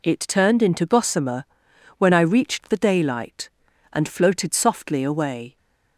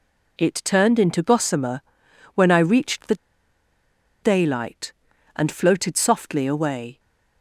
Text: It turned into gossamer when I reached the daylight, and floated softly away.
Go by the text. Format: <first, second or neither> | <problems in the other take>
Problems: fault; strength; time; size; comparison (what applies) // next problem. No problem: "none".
first | pauses between "gossamer" and "when"; noticeable; at 1.8 s; 0.54 s long; noticeable in the first // pauses between "the" and "daylight"; at 3.1 s; 1.0 s long